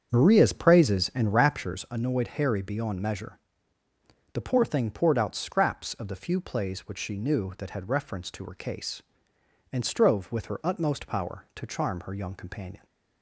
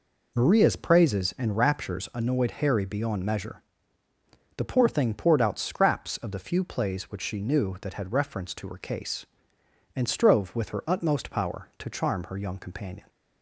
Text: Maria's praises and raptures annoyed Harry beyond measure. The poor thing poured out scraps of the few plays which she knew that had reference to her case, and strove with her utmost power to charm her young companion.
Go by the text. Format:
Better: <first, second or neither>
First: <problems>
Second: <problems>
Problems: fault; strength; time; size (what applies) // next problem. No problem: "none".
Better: second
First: starts louder than the rest; strong; until 1.7 s; 7.5 dB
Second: none